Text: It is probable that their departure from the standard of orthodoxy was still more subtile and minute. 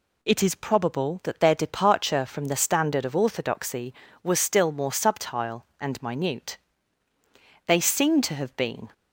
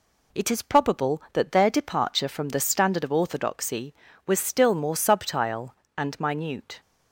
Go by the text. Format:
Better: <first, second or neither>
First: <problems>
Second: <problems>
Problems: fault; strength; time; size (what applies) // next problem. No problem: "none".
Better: second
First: goes on to say "They seem to have been"; noticeable; from 7.6 s on; 1.2 s long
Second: none